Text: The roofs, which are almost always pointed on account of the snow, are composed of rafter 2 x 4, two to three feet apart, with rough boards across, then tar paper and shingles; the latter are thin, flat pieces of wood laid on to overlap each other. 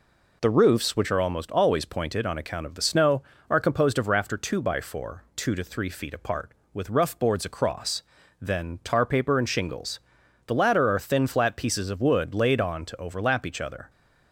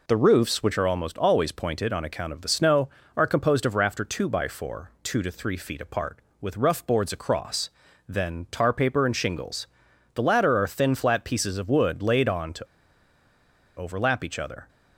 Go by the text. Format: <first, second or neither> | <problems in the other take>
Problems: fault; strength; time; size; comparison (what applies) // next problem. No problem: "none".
first | pauses between "to" and "overlap"; at 12.6 s; 1.1 s long